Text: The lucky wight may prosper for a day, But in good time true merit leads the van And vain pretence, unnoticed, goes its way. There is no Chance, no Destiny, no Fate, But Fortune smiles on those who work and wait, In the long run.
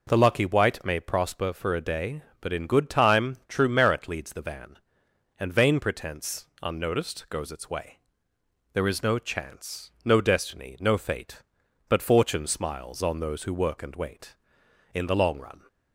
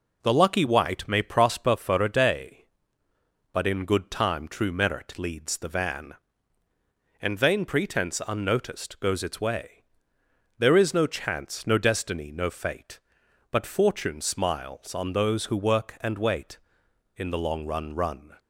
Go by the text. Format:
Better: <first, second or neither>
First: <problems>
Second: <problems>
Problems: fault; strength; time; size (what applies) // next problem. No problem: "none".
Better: first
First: none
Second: says "run" twice; at 17.9 s